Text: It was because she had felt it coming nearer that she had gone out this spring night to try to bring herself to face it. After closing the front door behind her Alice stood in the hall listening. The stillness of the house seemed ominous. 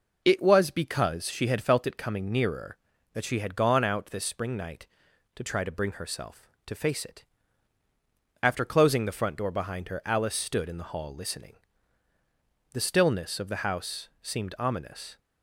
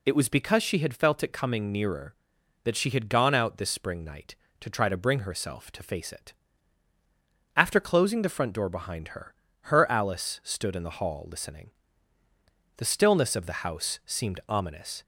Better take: first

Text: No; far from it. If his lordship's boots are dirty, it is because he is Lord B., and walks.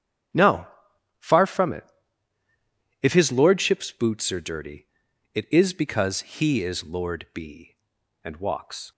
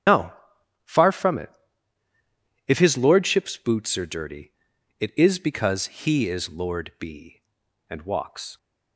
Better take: first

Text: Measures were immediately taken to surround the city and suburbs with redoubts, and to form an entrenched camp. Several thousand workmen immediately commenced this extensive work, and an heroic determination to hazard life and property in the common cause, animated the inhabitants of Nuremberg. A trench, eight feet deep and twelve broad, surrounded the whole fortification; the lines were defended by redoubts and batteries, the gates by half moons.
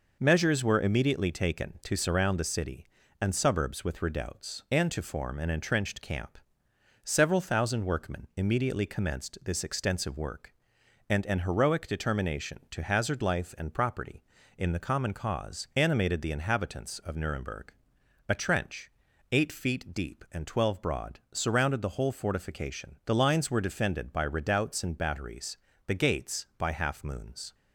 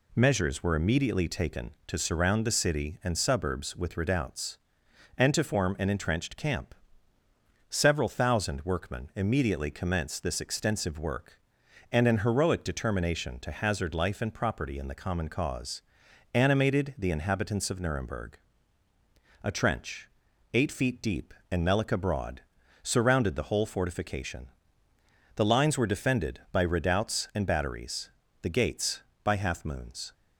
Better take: first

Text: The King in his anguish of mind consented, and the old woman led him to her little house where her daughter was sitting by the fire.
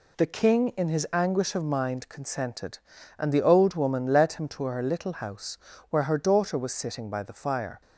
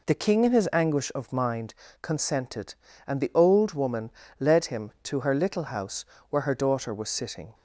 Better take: first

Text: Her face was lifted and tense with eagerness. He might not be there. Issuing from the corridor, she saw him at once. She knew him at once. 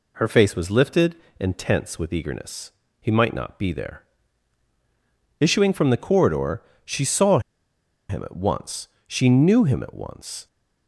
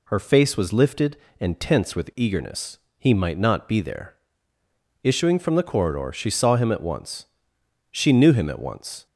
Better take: second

